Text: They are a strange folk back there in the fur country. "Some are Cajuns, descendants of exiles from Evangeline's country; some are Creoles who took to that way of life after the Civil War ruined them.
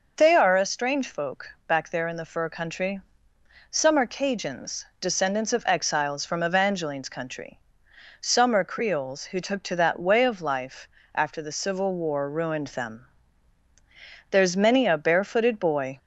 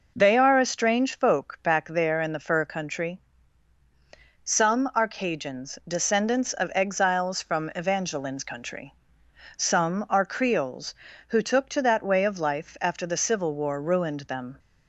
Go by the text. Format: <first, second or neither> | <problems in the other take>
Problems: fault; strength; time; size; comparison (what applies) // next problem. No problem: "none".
second | pauses between "folk" and "back"; slight; at 1.4 s; 0.18 s long // pauses between "life" and "after"; slight; at 10.8 s; 0.28 s long // goes on to say "There's many a barefooted boy"; from 14.3 s on; 1.6 s long